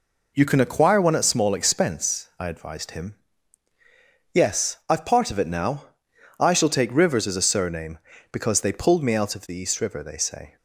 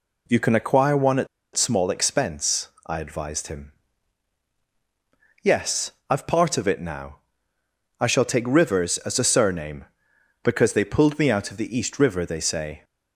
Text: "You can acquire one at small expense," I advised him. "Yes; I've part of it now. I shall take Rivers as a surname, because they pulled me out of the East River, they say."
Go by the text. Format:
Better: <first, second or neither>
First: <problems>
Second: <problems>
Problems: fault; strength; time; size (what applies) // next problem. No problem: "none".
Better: first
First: none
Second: pauses between "at" and "small"; slight; at 1.2 s; 0.28 s long